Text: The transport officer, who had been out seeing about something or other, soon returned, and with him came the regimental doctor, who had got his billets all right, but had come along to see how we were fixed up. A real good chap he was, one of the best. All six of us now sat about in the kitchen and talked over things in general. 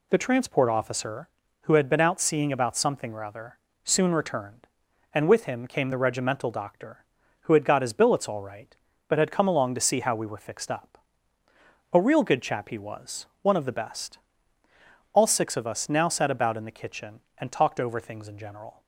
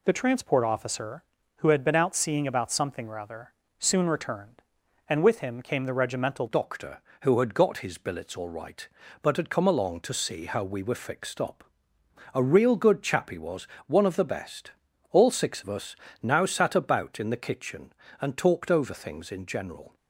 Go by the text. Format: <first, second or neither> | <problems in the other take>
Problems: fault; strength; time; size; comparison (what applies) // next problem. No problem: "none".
first | changes voice at "doctor"; from 6.4 s on; 13.5 s long // pauses between "us" and "now"; slight; at 15.9 s; 0.26 s long